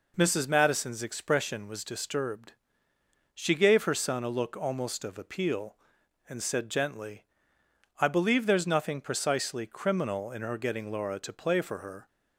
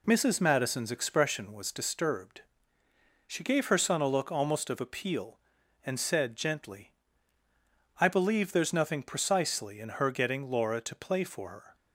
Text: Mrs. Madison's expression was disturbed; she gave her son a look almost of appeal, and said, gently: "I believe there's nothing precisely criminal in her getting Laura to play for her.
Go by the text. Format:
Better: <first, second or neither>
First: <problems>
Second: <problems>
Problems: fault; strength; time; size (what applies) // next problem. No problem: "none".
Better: first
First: none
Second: skips "criminal"; at 9.7 s